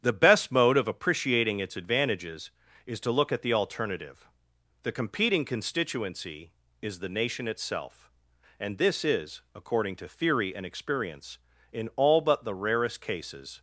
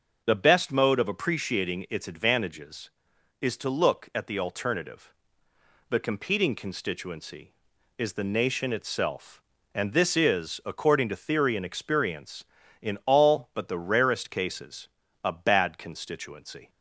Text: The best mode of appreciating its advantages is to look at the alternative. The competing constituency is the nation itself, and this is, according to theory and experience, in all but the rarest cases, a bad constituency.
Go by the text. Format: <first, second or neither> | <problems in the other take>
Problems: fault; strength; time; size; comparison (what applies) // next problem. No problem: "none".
second | starts louder than the rest; strong; until 1.0 s; 9 dB // stops before "a bad constituency"; at 13.5 s